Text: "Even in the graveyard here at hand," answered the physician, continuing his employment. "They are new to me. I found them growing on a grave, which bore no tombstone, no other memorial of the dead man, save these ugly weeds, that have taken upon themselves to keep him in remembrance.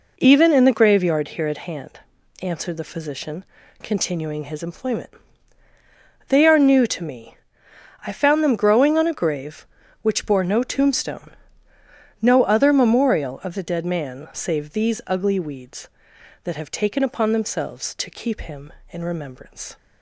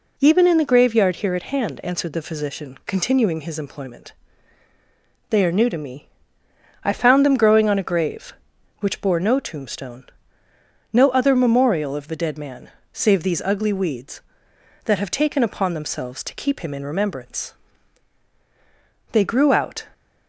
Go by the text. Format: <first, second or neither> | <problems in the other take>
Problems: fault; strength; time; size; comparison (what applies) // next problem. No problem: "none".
first | goes on to say "They grew out"; noticeable; from 19.1 s on; 0.74 s long